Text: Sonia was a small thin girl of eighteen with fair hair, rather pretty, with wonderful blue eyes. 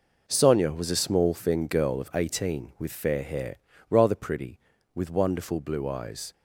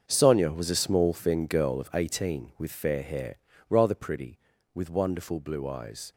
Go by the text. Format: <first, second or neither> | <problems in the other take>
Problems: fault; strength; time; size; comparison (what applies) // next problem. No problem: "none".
first | gets quieter; strong; throughout; 13 dB